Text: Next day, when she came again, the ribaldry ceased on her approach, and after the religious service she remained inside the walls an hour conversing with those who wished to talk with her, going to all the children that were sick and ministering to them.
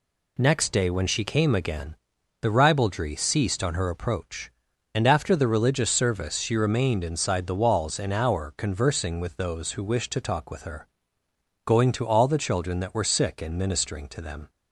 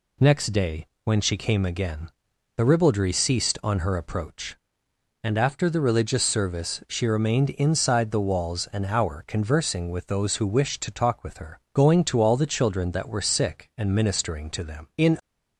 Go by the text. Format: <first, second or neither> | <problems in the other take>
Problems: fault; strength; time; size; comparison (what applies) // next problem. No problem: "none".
first | goes on to say "In"; slight; from 14.9 s on; 0.22 s long